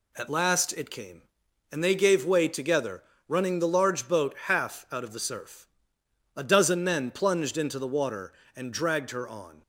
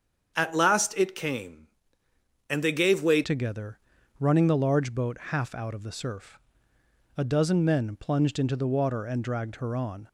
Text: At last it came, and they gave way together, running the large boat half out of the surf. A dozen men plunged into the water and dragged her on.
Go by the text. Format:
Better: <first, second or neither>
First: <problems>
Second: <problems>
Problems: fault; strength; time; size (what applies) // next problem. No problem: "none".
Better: first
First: none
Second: starts louder than the rest; strong; until 1.3 s; 7.5 dB // changes voice at "together"; from 3.2 s on; 6.8 s long